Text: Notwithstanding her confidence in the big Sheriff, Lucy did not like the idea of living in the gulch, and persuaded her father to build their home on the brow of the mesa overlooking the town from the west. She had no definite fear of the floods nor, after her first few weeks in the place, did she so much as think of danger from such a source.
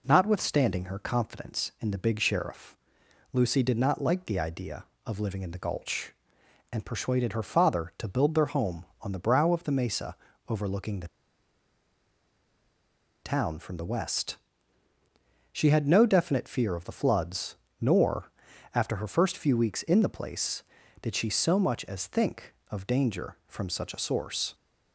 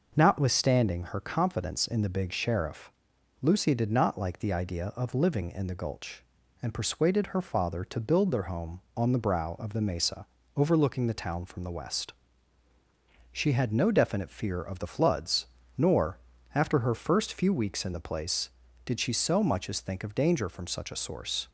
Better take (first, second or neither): second